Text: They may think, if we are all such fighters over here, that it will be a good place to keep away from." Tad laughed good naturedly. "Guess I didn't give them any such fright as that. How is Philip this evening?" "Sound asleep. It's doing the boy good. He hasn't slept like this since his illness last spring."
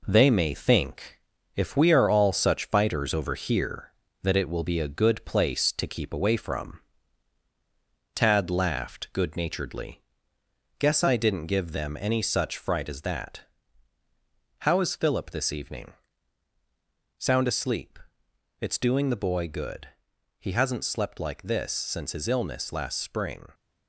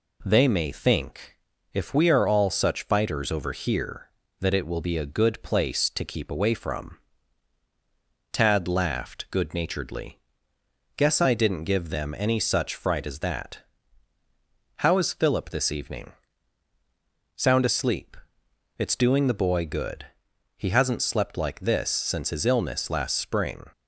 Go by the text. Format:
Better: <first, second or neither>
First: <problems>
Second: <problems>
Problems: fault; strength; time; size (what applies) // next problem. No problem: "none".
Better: second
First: gets quieter; noticeable; throughout; 5 dB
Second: none